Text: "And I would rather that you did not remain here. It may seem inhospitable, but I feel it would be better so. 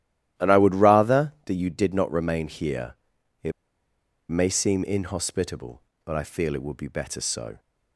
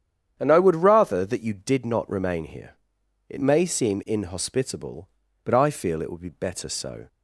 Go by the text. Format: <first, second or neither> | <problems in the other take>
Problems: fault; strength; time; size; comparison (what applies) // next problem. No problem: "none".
second | starts louder than the rest; strong; until 1.5 s; 13.5 dB; strong in the second // pauses between "It" and "may"; noticeable; at 3.5 s; 0.79 s long